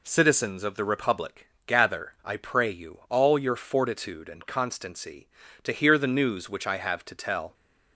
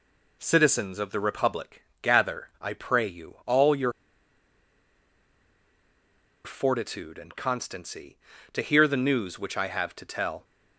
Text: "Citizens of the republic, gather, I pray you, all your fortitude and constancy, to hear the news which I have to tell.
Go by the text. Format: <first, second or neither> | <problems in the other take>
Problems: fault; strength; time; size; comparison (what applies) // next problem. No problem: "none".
first | pauses between "your" and "fortitude"; strong; at 3.9 s; 2.5 s long